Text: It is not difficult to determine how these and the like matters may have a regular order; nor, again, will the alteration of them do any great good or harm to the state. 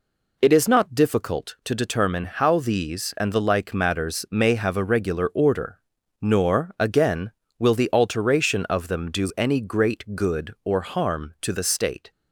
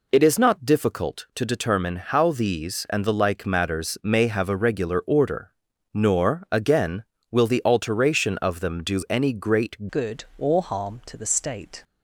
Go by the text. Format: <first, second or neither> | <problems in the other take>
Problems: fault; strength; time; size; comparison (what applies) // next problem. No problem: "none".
first | changes voice at "good"; from 9.9 s on; 1.9 s long